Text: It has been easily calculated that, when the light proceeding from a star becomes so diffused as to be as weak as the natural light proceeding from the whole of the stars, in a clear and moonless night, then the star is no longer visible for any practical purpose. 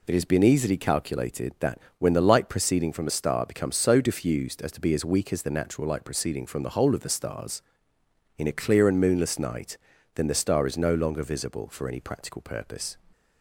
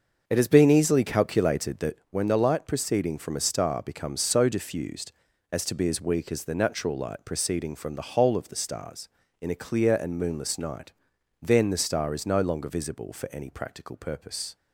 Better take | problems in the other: first | starts louder than the rest; until 2.0 s; 6.5 dB

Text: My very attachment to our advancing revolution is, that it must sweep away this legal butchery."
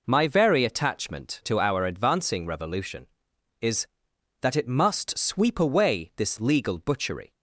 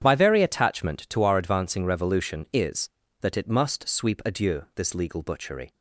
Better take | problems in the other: first | starts louder than the rest; strong; until 1.0 s; 9 dB // says "adieu" for "away"; at 4.2 s

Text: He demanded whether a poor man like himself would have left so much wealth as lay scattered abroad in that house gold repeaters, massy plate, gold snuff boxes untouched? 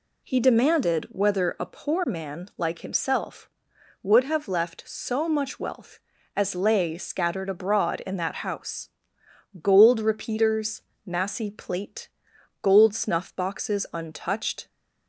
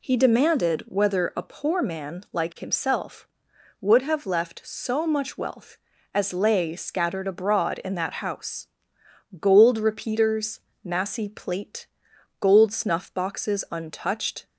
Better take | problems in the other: neither | pauses between "house" and "gold"; noticeable; the same in both

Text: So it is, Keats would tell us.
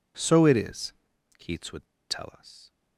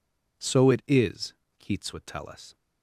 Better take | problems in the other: second | pauses between "would" and "tell"; slight; at 1.8 s; 0.26 s long

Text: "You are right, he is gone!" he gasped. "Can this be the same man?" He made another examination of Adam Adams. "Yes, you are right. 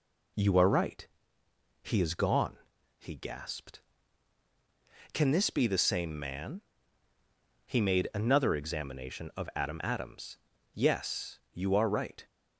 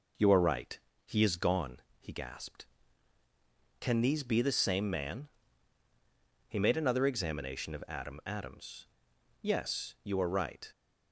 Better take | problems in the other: first | says "these" for "this"; at 4.0 s

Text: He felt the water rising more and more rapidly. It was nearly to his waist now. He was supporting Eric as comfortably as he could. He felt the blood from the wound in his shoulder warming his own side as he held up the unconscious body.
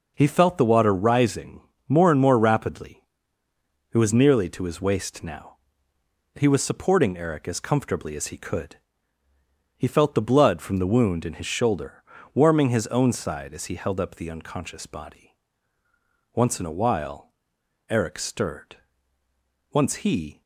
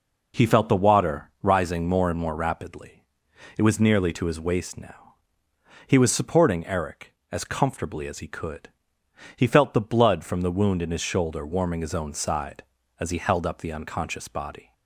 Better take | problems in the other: second | pauses between "rising" and "more"; slight; at 1.6 s; 0.28 s long // pauses between "shoulder" and "warming"; slight; at 12.0 s; 0.32 s long // goes on to say "Once in a while Eric stirred Once he"; strong; from 16.3 s on; 4.0 s long

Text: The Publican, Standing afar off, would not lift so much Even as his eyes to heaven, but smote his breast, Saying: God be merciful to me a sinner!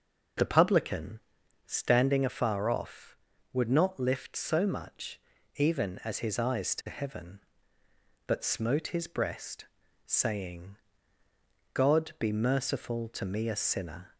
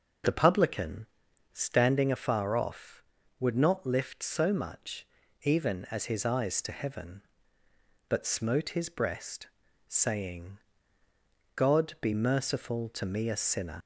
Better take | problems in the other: first | pauses between "much" and "Even"; at 5.0 s; 0.38 s long; also in the first // leaves "sinner" unfinished; at 13.8 s; 150 ms

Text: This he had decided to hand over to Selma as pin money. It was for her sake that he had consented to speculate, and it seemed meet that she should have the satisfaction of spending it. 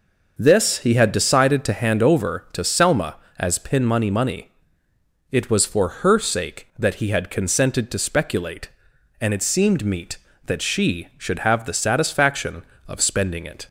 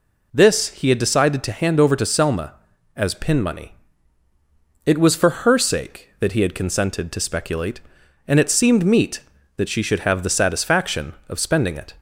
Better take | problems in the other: second | says "money" twice; at 4.1 s

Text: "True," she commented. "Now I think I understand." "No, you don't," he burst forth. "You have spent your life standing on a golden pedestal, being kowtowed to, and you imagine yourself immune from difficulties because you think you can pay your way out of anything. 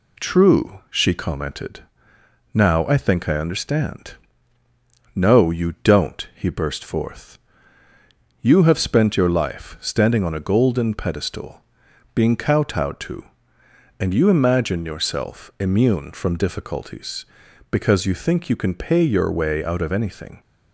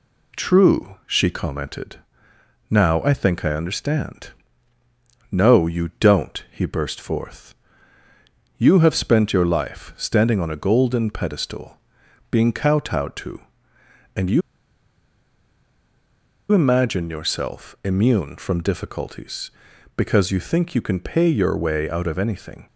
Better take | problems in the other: first | pauses between "you" and "imagine"; strong; at 14.4 s; 2.1 s long

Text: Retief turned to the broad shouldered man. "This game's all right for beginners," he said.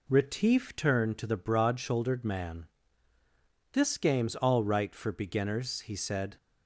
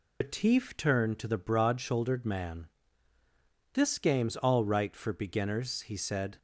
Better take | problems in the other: first | loses the start of "Retief"; at 0.2 s; 110 ms

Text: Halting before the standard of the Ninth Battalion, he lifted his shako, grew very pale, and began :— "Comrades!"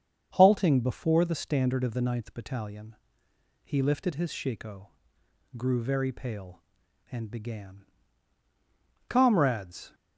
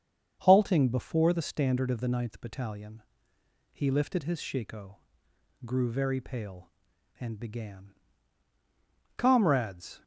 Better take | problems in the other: neither | starts louder than the rest; strong; the same in both

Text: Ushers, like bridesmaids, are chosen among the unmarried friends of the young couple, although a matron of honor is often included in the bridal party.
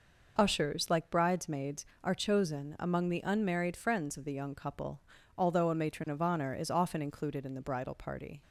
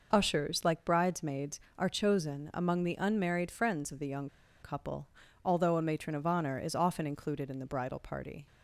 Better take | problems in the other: first | pauses between "young" and "couple"; slight; at 4.2 s; 0.34 s long

